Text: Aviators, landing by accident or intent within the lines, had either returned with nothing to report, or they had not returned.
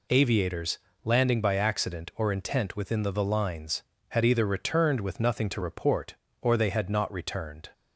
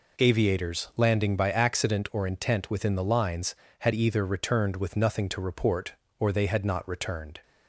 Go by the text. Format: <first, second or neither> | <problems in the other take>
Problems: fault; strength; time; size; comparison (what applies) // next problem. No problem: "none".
second | says "the" twice; at 3.0 s